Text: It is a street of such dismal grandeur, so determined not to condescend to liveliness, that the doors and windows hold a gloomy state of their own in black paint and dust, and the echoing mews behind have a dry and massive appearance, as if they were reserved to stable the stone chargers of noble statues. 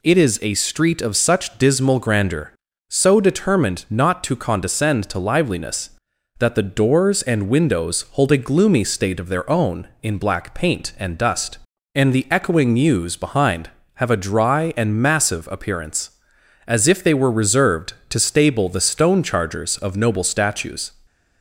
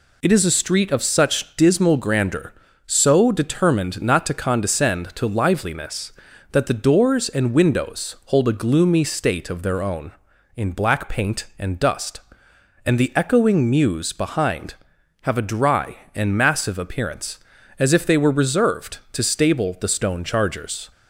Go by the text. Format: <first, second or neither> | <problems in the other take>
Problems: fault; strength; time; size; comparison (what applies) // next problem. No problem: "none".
first | stops before "of noble statues"; at 20.9 s